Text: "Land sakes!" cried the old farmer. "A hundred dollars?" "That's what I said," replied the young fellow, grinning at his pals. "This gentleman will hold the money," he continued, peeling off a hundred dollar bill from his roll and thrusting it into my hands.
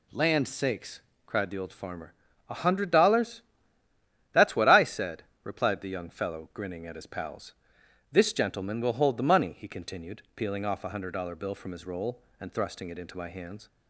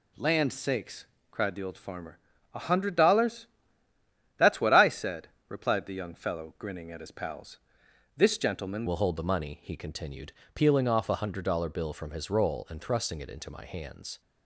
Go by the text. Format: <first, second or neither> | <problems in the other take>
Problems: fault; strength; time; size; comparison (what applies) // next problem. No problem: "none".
first | changes voice at "will"; from 8.8 s on; 5.3 s long